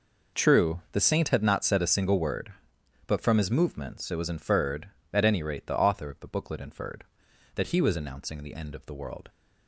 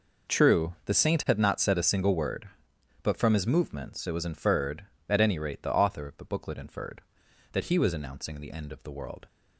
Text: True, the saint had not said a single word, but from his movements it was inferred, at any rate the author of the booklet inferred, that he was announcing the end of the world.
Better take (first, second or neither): neither